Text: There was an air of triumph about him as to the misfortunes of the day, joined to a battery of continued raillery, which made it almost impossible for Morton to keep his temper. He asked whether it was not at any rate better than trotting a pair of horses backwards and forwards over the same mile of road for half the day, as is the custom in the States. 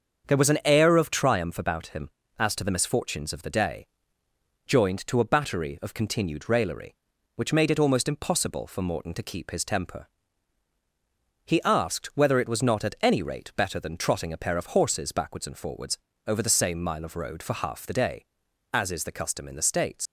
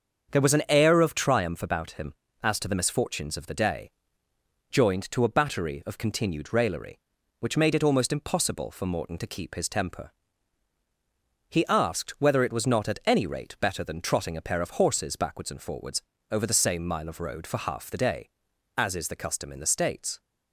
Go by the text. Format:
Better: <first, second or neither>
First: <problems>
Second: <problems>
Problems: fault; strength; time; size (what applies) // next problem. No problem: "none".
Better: second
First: starts louder than the rest; strong; until 1.3 s; 7 dB // pauses between "forwards" and "over"; slight; at 15.9 s; 0.30 s long // leaves "States" unfinished; at 20.0 s; 100 ms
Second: starts louder than the rest; strong; until 1.3 s; 7 dB // pauses between "forwards" and "over"; slight; at 15.9 s; 0.30 s long